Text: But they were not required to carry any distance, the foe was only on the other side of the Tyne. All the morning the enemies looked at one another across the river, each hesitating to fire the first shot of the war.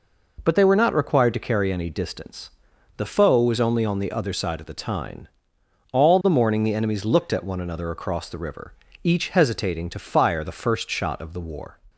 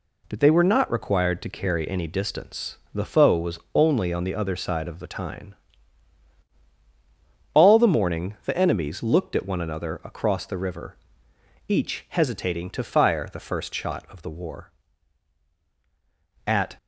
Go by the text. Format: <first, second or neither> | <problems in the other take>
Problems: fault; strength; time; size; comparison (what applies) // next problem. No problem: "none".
first | goes on to say "At"; slight; from 16.4 s on; 0.30 s long